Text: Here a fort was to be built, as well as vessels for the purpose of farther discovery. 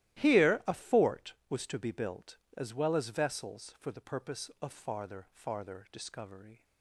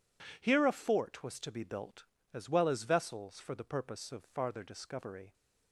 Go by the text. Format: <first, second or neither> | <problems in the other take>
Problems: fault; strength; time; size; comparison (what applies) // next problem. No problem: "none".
second | starts louder than the rest; strong; until 1.2 s; 14.5 dB // says "farther" twice; at 5.2 s